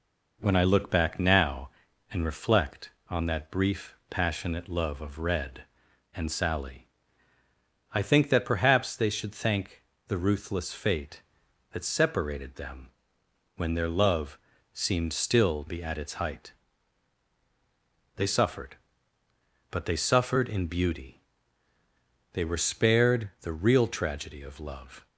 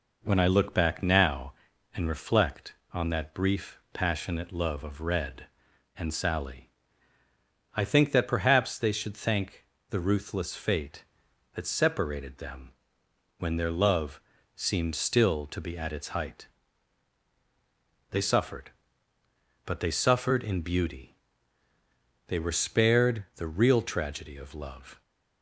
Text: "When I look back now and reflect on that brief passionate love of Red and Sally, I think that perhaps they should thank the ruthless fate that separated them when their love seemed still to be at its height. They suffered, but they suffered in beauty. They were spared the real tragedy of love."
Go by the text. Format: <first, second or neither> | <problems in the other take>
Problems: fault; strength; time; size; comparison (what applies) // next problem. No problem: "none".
second | pauses between "thank" and "the"; slight; at 9.8 s; 0.24 s long; slight in the second // pauses between "them" and "when"; noticeable; at 12.8 s; 0.68 s long; noticeable in the second // pauses between "love" and "seemed"; slight; at 14.3 s; 0.32 s long; slight in the second // skips "to"; at 15.6 s